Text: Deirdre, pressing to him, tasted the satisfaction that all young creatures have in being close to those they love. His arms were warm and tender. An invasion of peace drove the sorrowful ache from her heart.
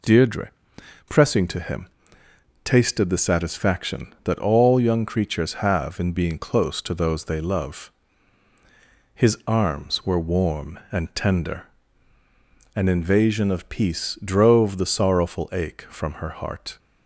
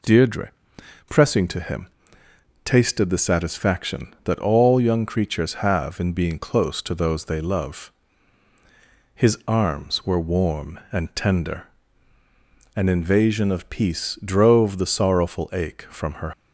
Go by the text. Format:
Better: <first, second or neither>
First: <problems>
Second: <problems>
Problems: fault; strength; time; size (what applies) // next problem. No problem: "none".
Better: first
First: none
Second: stops before "heart"; at 16.3 s